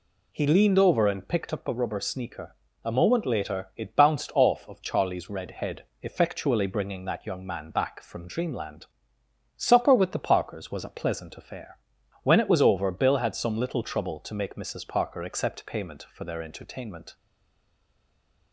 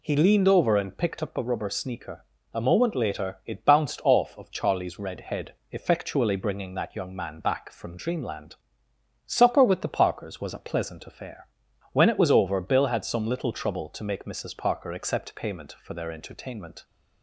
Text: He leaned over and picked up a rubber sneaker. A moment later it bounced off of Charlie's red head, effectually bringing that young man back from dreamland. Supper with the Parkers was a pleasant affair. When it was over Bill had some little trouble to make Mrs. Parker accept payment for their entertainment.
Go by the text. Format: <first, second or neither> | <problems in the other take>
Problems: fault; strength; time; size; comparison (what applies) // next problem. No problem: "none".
second | stays silent after the last word; noticeable; from 17.1 s on; 1.4 s long